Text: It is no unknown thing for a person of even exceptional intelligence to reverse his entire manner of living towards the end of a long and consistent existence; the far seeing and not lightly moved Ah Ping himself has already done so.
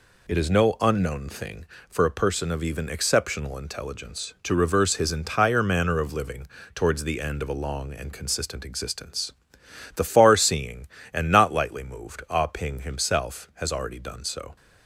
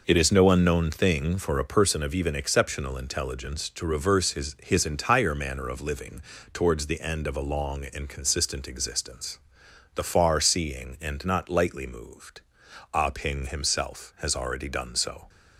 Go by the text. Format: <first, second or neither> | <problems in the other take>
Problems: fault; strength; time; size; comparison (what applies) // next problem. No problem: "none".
first | says "his" twice; at 4.6 s // pauses between "living" and "towards"; slight; at 6.2 s; 0.32 s long; slight in the first // pauses between "moved" and "Ah"; noticeable; at 12.4 s; 0.52 s long